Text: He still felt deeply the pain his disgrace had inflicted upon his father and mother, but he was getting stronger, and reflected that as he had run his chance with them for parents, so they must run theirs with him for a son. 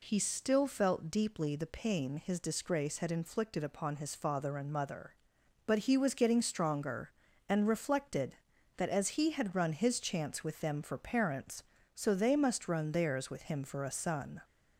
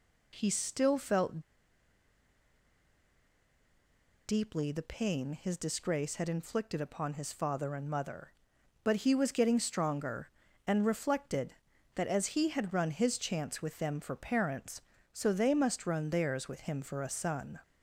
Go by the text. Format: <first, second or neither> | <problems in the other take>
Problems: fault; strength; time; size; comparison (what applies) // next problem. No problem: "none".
first | pauses between "felt" and "deeply"; strong; at 1.3 s; 2.8 s long